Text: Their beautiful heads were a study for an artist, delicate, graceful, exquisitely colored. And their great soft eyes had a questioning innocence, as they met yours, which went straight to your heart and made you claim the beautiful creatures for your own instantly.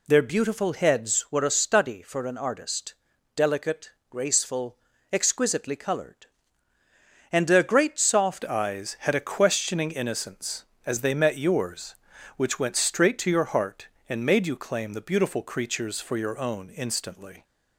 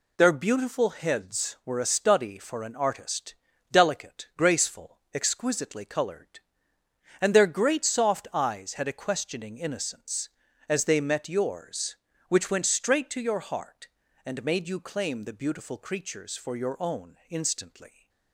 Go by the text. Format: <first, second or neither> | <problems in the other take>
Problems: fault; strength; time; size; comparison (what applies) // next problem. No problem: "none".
second | changes voice at "eyes"; from 8.4 s on; 9.0 s long